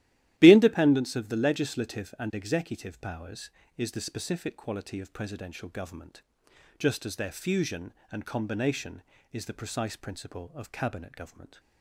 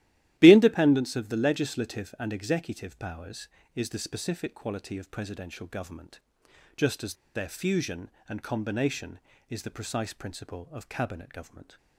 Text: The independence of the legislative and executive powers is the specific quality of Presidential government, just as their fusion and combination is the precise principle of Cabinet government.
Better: first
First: starts louder than the rest; strong; until 1.3 s; 14 dB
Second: starts louder than the rest; strong; until 1.4 s; 14 dB // pauses between "as" and "their"; slight; at 7.1 s; 0.19 s long

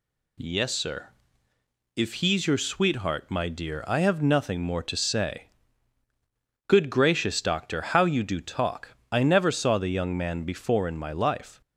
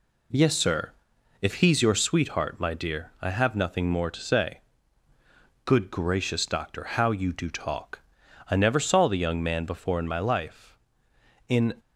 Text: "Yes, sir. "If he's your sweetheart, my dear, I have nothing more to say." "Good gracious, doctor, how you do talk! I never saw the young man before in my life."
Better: first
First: none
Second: goes on to say "In"; slight; from 11.4 s on; 0.24 s long

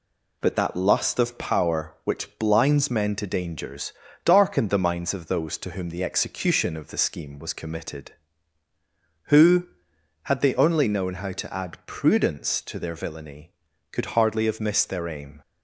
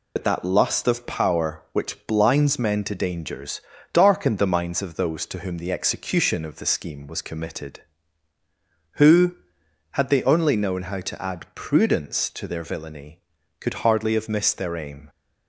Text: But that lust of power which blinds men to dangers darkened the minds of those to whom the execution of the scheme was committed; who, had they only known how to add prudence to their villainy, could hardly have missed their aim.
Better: first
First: pauses between "dangers" and "darkened"; slight; at 3.9 s; 0.34 s long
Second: loses the start of "But"; at 0.1 s; 65 ms // pauses between "dangers" and "darkened"; slight; at 3.5 s; 0.34 s long

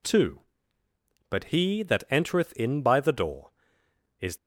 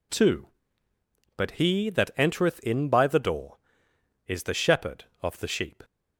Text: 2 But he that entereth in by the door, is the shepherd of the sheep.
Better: second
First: stops before "the shepherd of the sheep"; at 4.3 s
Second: none

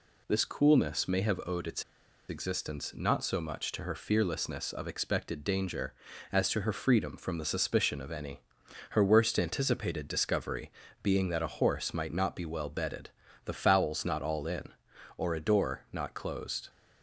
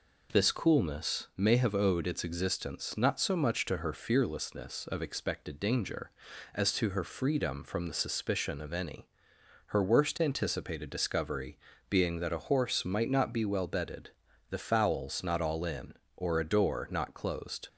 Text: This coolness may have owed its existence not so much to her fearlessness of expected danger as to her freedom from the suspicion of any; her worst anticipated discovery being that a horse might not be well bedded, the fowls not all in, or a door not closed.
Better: second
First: pauses between "its" and "existence"; noticeable; at 1.8 s; 0.46 s long // pauses between "discovery" and "being"; slight; at 10.6 s; 0.32 s long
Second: pauses between "discovery" and "being"; slight; at 11.5 s; 0.32 s long

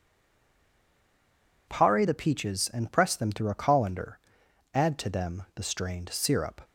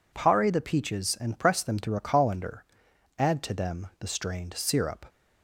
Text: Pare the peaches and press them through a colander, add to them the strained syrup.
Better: second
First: stays silent before the first word; noticeable; until 1.6 s; 1.6 s long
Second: none

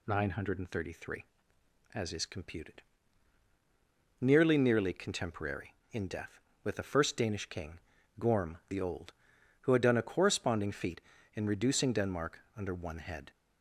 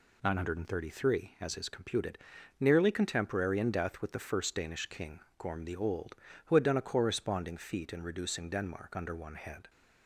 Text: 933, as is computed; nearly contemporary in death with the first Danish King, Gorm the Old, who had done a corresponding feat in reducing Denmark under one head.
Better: second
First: says "nearly" twice; at 4.5 s // pauses between "Denmark" and "under"; slight; at 12.4 s; 0.16 s long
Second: none

